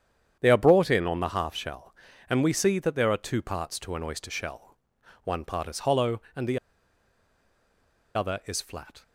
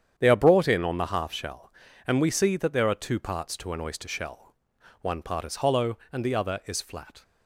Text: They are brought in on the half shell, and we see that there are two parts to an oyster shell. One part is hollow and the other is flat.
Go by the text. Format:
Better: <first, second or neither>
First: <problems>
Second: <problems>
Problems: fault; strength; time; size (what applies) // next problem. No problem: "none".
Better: second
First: starts louder than the rest; strong; until 1.4 s; 9 dB // pauses between "the" and "other"; strong; at 6.5 s; 1.5 s long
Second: starts louder than the rest; strong; until 1.2 s; 8.5 dB